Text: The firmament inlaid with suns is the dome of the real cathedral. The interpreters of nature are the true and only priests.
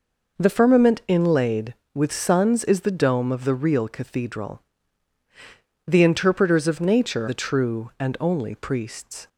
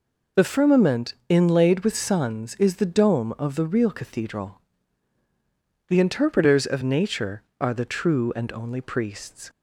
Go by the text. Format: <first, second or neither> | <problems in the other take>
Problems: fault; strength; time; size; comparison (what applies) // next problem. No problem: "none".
second | skips "are"; at 7.2 s